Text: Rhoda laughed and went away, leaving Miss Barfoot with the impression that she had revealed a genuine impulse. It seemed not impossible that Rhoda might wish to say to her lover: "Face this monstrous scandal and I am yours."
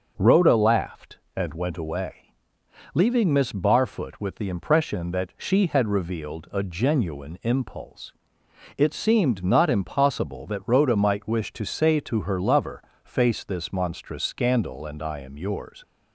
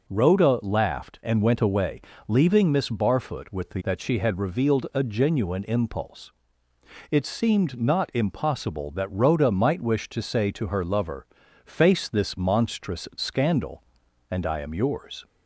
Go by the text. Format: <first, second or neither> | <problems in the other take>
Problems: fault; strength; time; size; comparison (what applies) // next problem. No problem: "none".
first | skips "impression"; at 3.8 s